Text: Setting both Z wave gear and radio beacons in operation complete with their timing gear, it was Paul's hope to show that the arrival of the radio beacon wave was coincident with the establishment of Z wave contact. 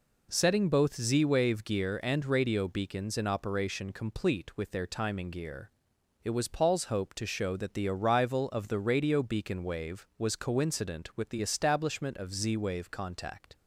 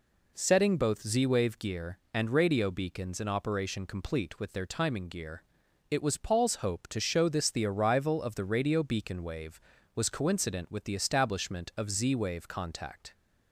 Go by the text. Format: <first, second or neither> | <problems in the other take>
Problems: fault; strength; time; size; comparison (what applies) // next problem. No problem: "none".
first | says "this" for "that"; at 7.2 s